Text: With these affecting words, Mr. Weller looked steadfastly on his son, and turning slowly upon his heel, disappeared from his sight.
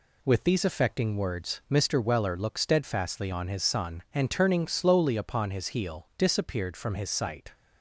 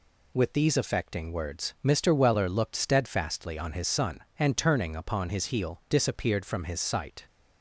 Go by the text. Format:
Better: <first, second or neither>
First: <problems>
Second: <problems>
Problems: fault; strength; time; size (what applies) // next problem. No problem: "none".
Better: first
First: none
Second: skips "slowly"; at 4.9 s